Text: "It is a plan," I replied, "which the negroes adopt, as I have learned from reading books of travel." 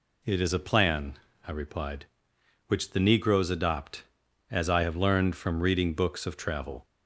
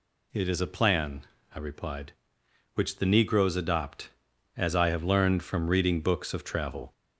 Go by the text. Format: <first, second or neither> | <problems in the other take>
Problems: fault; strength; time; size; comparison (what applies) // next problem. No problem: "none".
first | gets louder; slight; throughout; 2 dB